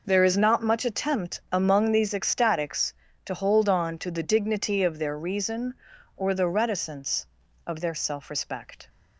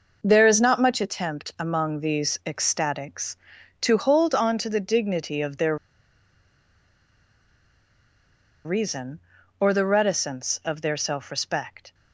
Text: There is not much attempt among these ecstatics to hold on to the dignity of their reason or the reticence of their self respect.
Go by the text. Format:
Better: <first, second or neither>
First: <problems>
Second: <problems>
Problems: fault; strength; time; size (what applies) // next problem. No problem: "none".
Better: first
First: none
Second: pauses between "their" and "reason"; strong; at 5.7 s; 2.8 s long